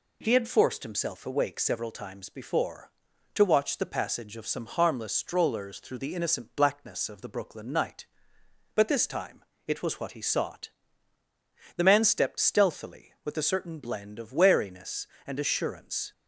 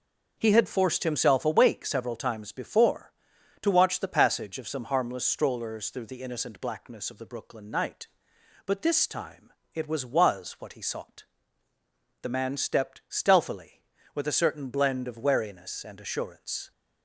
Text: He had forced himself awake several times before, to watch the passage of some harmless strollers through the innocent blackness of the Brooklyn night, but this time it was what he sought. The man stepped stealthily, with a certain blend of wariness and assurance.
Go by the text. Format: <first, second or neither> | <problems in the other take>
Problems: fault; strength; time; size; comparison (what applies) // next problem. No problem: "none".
first | starts louder than the rest; noticeable; until 1.3 s; 6 dB // pauses between "time" and "it"; slight; at 9.5 s; 0.24 s long; slight in the first // says "was" twice; at 10.0 s